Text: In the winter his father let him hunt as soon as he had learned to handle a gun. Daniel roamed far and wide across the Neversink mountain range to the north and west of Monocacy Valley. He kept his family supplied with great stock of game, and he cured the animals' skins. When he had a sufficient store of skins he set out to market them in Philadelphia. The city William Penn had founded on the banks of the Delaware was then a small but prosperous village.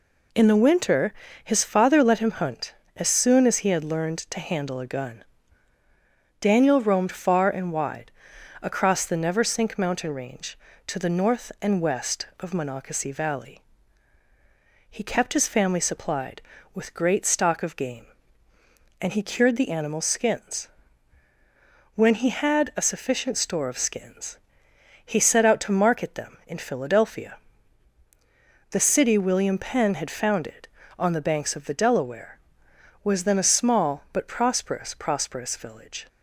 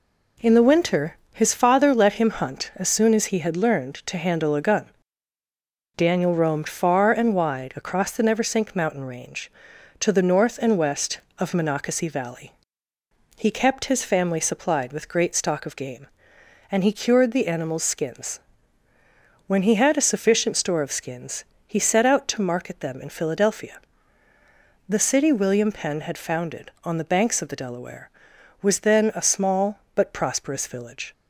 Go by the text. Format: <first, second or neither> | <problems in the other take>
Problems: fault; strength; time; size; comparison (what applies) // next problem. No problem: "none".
second | pauses between "winter" and "his"; slight; at 1.1 s; 0.30 s long; slight in the second // pauses between "wide" and "across"; noticeable; at 8.1 s; 0.52 s long // pauses between "skins" and "he"; noticeable; at 24.3 s; 0.68 s long; slight in the second // says "prosperous" twice; at 34.9 s